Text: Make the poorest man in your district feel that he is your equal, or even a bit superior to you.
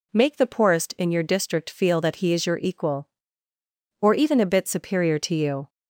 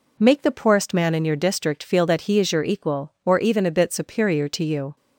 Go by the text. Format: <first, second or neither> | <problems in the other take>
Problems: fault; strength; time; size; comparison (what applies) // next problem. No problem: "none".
second | skips "man"; at 0.9 s